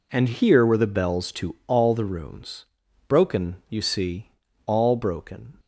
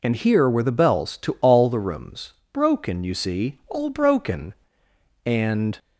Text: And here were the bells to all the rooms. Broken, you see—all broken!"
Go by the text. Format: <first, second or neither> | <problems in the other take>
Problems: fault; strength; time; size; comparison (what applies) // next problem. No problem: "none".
first | goes on to say "And"; from 5.2 s on; 0.52 s long